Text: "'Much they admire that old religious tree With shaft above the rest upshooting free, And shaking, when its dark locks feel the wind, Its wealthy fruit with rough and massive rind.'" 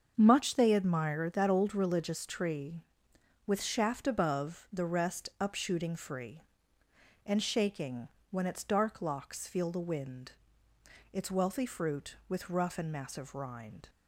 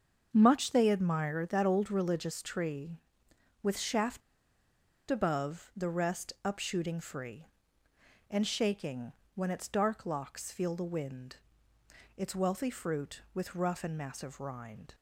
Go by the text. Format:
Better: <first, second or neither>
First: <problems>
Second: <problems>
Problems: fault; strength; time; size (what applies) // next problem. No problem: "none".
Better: first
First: starts louder than the rest; until 1.1 s; 7 dB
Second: starts louder than the rest; until 1.3 s; 7 dB // pauses between "shaft" and "above"; noticeable; at 4.2 s; 0.89 s long